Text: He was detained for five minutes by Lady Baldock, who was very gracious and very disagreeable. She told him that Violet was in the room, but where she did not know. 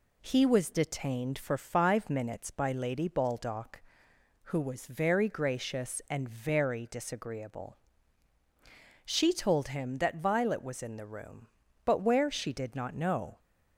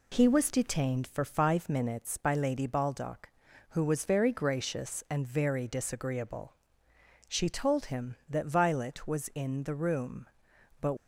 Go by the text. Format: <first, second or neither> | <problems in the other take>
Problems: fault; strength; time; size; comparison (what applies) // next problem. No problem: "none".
first | stops before "where she did not know"; at 10.9 s